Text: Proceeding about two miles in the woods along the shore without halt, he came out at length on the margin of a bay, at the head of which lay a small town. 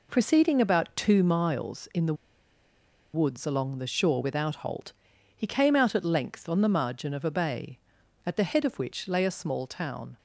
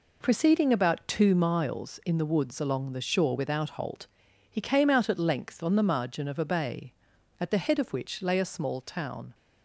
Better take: second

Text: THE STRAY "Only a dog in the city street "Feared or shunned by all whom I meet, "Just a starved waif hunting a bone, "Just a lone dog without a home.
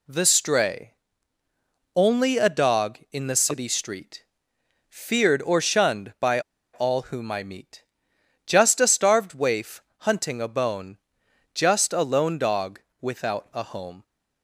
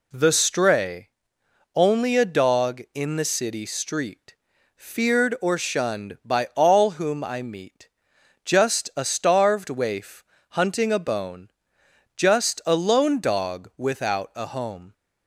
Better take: second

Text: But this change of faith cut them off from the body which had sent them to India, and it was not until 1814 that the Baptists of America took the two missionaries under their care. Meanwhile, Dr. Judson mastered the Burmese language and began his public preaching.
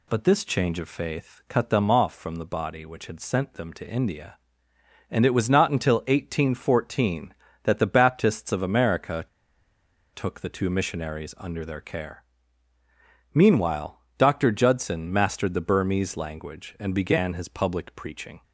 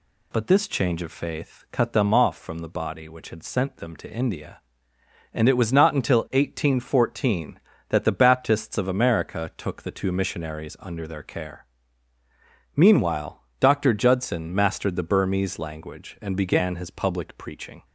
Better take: second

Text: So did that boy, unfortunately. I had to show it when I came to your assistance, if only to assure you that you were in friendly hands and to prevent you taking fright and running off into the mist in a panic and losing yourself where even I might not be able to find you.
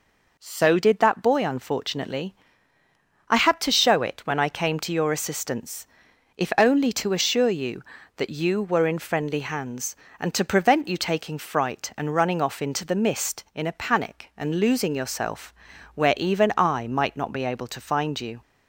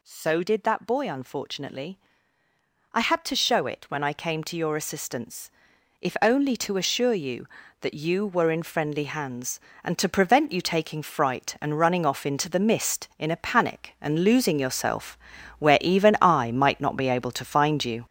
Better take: first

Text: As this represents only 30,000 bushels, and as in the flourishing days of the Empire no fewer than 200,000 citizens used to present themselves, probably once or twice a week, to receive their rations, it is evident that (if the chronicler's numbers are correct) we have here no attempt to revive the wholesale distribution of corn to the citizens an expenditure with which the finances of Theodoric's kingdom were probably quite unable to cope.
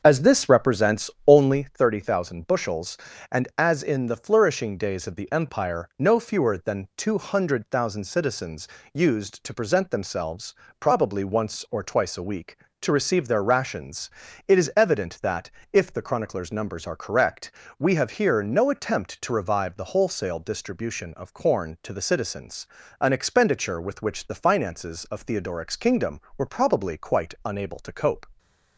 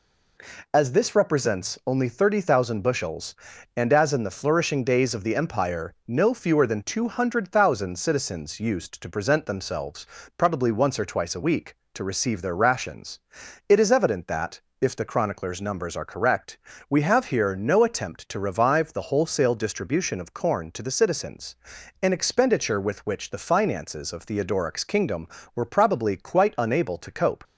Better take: second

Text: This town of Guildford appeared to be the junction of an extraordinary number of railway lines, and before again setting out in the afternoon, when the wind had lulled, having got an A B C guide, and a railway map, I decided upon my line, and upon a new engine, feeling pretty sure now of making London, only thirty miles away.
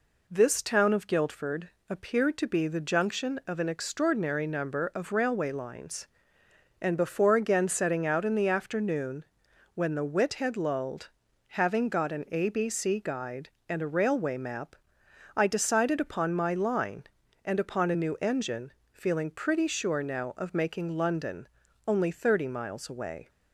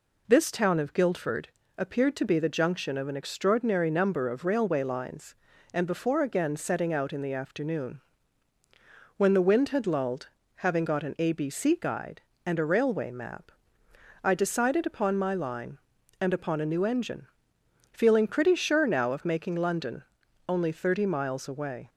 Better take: second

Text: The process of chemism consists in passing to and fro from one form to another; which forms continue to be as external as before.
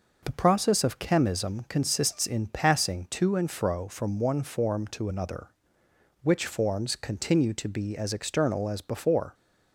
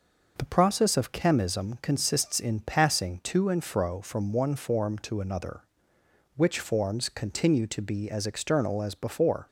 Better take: neither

